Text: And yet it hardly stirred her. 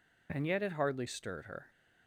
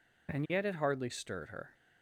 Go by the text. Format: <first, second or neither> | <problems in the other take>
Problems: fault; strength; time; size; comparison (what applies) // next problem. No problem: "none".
neither | none